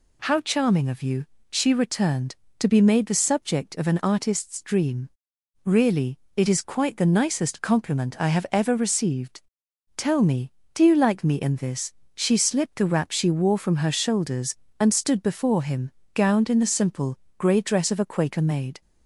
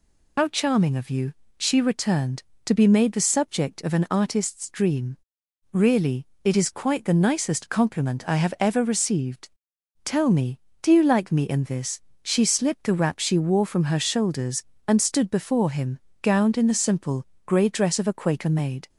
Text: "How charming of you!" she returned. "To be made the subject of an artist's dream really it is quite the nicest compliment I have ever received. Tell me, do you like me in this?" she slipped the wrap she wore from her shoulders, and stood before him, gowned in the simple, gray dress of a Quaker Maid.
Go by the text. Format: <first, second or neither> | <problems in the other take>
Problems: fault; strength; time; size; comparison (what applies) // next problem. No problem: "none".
first | loses the start of "How"; at 0.3 s; 85 ms // pauses between "dream" and "really"; noticeable; at 5.1 s; 0.54 s long; noticeable in the first // pauses between "really" and "it"; slight; at 6.2 s; 0.16 s long; slight in the first